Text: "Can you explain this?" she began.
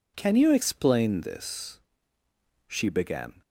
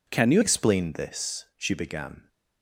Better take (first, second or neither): first